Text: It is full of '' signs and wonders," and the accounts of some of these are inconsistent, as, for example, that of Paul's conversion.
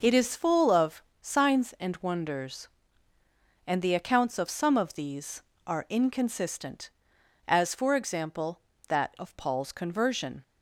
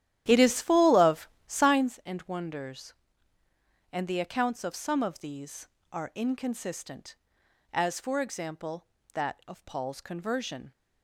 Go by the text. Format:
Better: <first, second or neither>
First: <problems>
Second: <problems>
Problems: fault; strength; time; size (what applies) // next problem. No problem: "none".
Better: first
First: none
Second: starts louder than the rest; strong; until 1.9 s; 11.5 dB